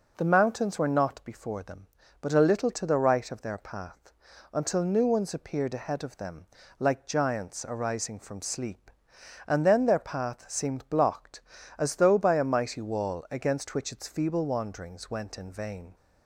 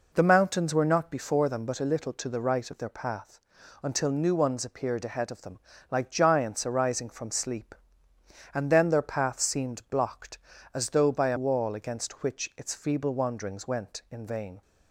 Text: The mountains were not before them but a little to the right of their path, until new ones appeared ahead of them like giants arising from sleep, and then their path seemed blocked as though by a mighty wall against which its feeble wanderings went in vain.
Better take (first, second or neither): first